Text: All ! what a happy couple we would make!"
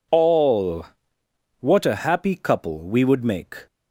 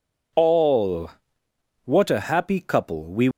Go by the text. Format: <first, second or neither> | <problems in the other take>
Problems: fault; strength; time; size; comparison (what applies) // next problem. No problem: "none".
first | stops before "would make"; at 3.3 s